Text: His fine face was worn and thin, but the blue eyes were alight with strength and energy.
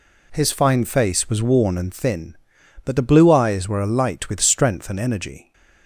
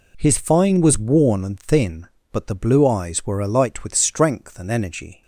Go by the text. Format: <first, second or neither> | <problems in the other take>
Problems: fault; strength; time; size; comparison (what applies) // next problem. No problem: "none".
first | skips "face"; at 0.7 s